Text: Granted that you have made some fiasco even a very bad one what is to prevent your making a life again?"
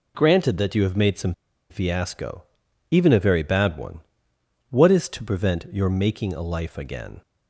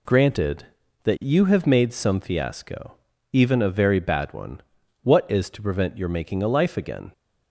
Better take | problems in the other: second | pauses between "some" and "fiasco"; slight; at 1.3 s; 0.36 s long // pauses between "fiasco" and "even"; noticeable; at 2.4 s; 0.50 s long; also in the second // pauses between "one" and "what"; noticeable; at 4.0 s; 0.68 s long; also in the second

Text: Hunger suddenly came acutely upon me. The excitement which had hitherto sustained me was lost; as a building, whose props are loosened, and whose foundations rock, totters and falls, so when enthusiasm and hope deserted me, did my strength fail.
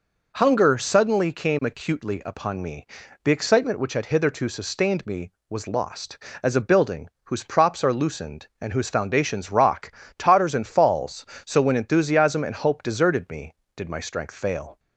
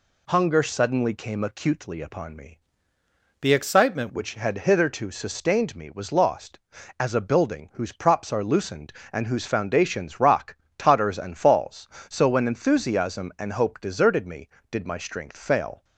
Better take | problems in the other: first | changes voice from "The" to "excitement"; from 3.4 to 4.0 s; 0.6 s long

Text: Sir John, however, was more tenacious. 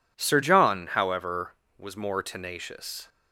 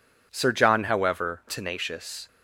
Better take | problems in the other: first | skips "was more"; at 1.4 s

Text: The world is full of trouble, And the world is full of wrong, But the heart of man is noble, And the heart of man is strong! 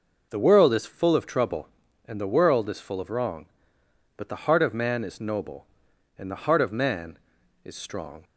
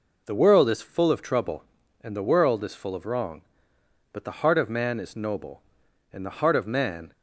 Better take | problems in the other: first | stops before "is strong"; at 7.1 s

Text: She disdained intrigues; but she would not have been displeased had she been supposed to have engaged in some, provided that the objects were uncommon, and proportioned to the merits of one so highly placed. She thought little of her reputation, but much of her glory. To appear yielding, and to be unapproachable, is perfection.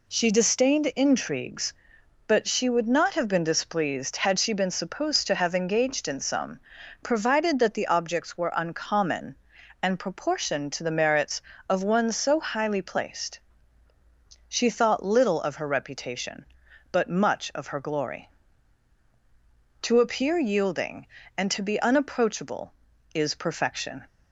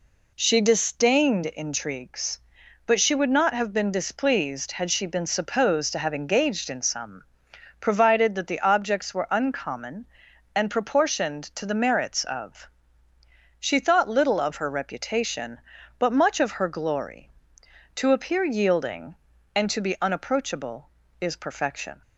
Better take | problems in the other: first | skips "one so highly placed"; at 13.1 s

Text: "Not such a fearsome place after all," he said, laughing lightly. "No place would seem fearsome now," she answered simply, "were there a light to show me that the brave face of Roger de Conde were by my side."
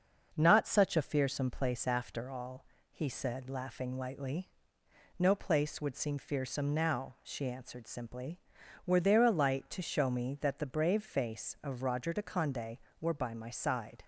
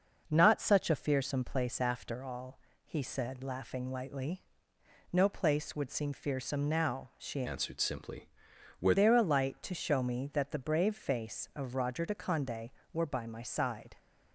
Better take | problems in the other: first | starts louder than the rest; noticeable; until 1.3 s; 6 dB; also in the first // changes voice from "answered" to "were"; from 7.4 to 8.9 s; 1.5 s long

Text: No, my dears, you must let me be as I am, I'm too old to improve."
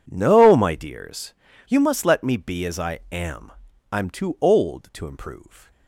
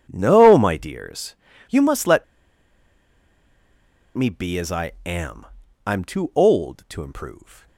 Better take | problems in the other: first | pauses between "let" and "me"; strong; at 2.2 s; 1.9 s long

